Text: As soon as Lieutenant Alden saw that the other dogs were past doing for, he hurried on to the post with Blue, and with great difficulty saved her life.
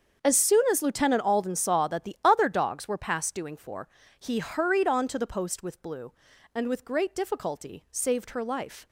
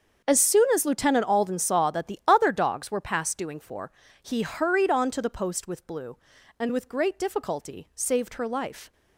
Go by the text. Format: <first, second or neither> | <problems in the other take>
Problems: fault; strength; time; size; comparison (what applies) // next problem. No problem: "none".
neither | starts louder than the rest; the same in both